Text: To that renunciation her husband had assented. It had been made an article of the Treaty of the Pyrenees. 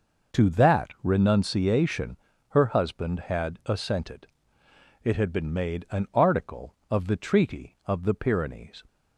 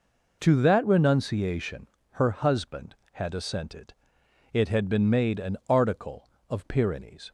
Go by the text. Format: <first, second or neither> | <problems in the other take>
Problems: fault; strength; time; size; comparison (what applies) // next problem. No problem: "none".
first | pauses between "renunciation" and "her"; slight; at 1.8 s; 0.24 s long; slight in the first // skips "the Treaty of the"; at 6.6 s